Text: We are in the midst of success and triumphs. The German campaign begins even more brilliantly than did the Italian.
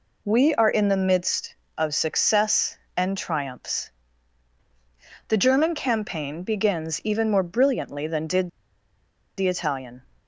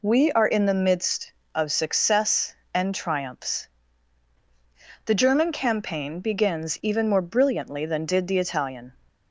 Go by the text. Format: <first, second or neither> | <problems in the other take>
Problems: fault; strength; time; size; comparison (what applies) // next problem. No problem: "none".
second | pauses between "did" and "the"; noticeable; at 8.4 s; 0.90 s long